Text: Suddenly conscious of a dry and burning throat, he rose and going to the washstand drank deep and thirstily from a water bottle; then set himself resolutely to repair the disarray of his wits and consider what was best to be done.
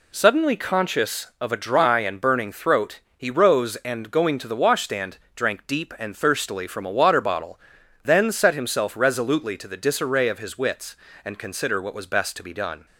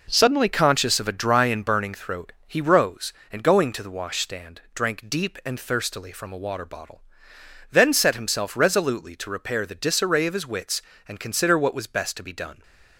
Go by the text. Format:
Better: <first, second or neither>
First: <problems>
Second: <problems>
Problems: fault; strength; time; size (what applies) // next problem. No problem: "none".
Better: second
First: pauses between "washstand" and "drank"; slight; at 5.1 s; 0.16 s long // skips "repair"; at 9.6 s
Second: none